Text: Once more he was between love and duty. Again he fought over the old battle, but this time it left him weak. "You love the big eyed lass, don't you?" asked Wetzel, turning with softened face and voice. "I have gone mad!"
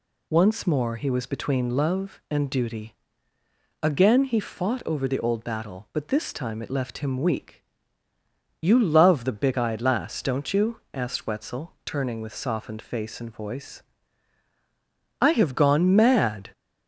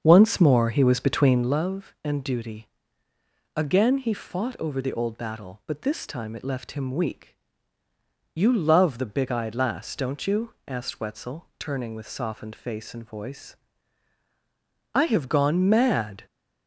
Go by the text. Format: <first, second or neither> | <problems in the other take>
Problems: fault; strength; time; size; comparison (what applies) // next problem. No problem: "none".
first | starts louder than the rest; until 1.6 s; 7 dB